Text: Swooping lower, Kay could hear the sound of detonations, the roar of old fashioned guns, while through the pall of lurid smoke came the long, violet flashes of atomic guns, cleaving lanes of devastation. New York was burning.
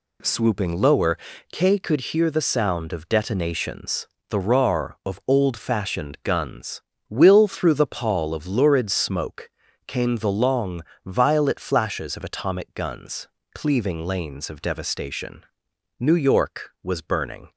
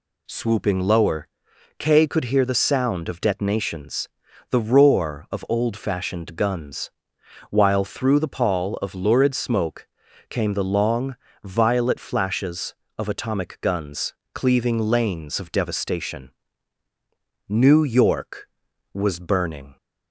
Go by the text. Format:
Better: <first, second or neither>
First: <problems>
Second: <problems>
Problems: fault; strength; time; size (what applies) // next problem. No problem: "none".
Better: second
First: says "will" for "while"; at 7.0 s // pauses between "smoke" and "came"; at 9.4 s; 0.38 s long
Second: pauses between "smoke" and "came"; at 9.8 s; 0.42 s long